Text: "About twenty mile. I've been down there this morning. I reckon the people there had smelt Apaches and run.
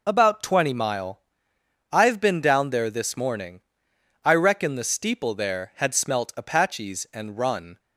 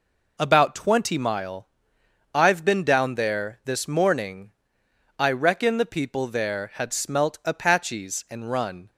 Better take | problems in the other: second | says "steeple" for "people"; at 4.8 s

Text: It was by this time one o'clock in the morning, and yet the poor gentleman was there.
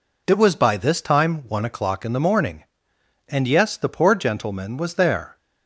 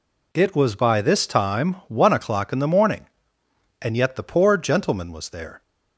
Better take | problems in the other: second | says "yes" for "yet"; at 3.4 s

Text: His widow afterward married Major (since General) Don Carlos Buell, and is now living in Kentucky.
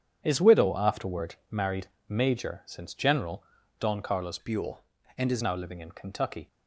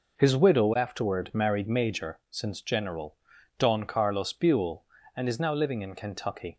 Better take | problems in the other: second | starts louder than the rest; strong; until 1.2 s; 8.5 dB // pauses between "afterward" and "married"; slight; at 1.3 s; 0.16 s long // pauses between "married" and "Major"; slight; at 1.8 s; 0.20 s long // changes voice from "Buell" to "is"; from 4.3 to 5.4 s; 1.1 s long

